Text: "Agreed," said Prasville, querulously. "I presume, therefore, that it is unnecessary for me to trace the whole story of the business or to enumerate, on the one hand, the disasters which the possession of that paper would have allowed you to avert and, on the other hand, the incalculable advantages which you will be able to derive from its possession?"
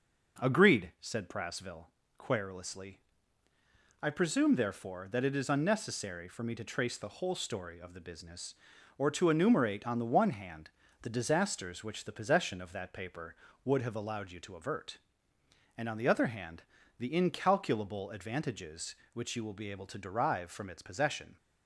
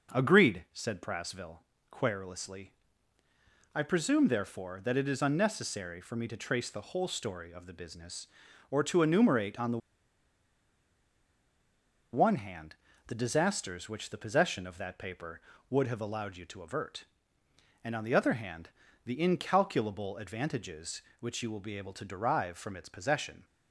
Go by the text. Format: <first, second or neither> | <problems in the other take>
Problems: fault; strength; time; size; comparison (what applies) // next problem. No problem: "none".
first | pauses between "the" and "one"; strong; at 9.7 s; 2.3 s long